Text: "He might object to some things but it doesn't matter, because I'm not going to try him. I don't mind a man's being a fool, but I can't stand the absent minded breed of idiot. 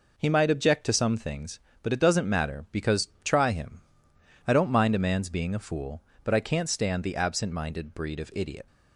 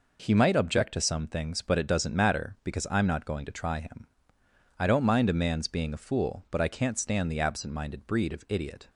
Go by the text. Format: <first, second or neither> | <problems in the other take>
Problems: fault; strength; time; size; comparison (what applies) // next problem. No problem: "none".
second | skips "I'm not going to"; at 3.1 s